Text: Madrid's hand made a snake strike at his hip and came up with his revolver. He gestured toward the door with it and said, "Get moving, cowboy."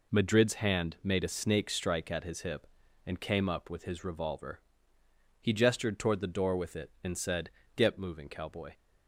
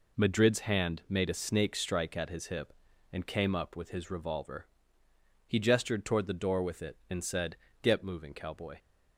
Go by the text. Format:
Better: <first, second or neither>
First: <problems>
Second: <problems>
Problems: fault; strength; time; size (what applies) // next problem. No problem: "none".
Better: neither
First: none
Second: none